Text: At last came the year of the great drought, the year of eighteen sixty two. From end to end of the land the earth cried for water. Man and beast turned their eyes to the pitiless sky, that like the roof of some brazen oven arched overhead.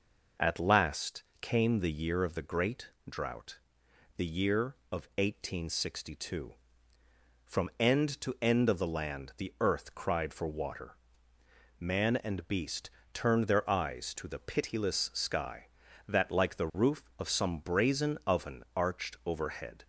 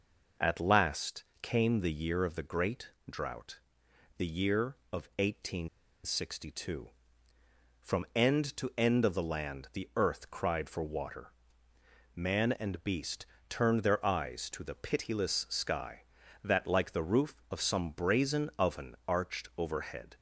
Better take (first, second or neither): first